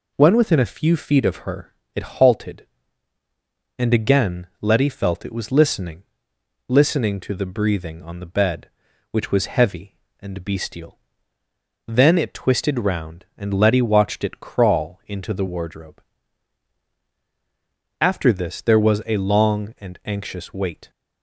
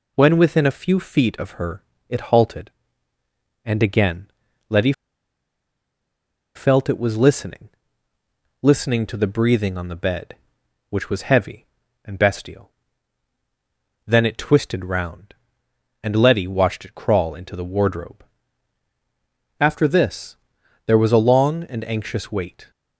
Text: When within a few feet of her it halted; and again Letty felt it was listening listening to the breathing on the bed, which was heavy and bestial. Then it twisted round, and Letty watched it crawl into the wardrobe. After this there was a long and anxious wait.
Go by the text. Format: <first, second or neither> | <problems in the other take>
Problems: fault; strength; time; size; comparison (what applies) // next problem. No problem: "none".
first | pauses between "her" and "it"; slight; at 1.8 s; 0.26 s long; slight in the first // pauses between "again" and "Letty"; at 4.2 s; 0.40 s long; slight in the first // pauses between "Letty" and "felt"; strong; at 4.9 s; 1.6 s long // pauses between "listening" and "listening"; noticeable; at 7.6 s; 0.94 s long; noticeable in the first // pauses between "this" and "there"; noticeable; at 20.3 s; 0.50 s long